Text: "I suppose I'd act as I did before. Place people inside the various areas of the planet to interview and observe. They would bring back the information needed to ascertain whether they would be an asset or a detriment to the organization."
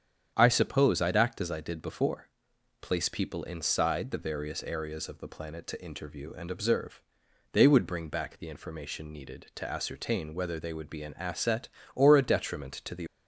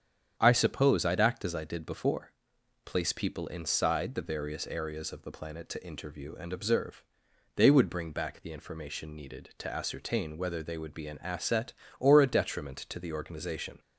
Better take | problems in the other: second | starts louder than the rest; strong; until 1.3 s; 8.5 dB; strong in the second // stops before "organization"; at 13.0 s

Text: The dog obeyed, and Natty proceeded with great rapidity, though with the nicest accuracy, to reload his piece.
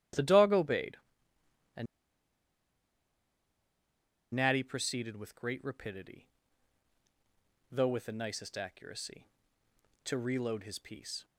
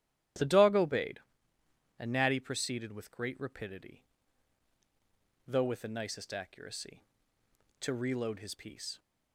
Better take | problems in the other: second | starts louder than the rest; strong; until 4.4 s; 12 dB; strong in the second // pauses between "and" and "Natty"; strong; at 1.8 s; 2.4 s long

